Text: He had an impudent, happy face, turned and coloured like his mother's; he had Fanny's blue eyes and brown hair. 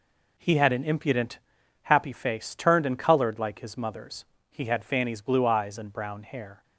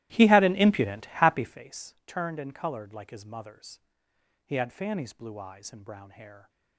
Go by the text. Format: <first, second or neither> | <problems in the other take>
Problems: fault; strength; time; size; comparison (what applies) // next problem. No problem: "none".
first | starts louder than the rest; strong; until 1.7 s; 15.5 dB